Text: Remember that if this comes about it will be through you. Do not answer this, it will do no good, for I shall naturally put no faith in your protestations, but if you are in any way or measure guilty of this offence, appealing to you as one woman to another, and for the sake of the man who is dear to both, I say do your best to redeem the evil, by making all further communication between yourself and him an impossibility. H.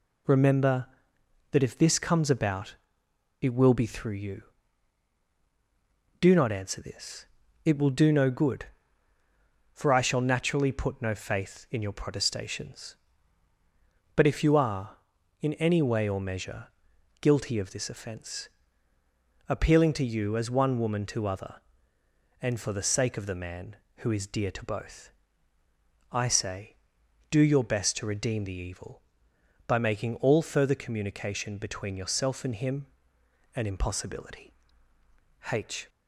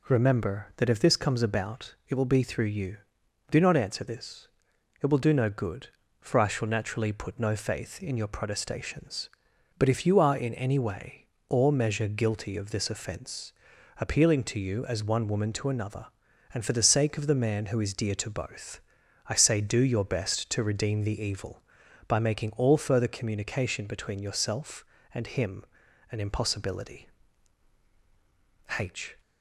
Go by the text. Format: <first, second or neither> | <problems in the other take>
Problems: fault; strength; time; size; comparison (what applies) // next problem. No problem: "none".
second | pauses between "about" and "it"; noticeable; at 2.7 s; 0.66 s long // pauses between "measure" and "guilty"; noticeable; at 16.6 s; 0.54 s long // says "other" for "another"; at 21.2 s // pauses between "him" and "an"; noticeable; at 32.8 s; 0.70 s long; noticeable in the second